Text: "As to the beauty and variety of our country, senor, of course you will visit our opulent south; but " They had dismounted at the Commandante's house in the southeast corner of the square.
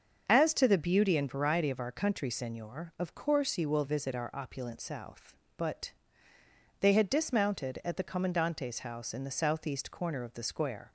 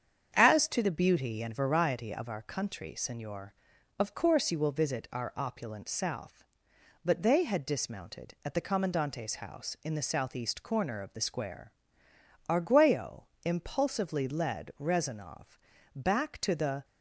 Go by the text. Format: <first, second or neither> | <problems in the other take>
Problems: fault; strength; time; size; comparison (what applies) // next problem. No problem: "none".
first | starts louder than the rest; strong; until 1.3 s; 8 dB; also in the first // goes on to say "Arguello impulsively led Rezanov back to the"; strong; from 12.4 s on; 4.3 s long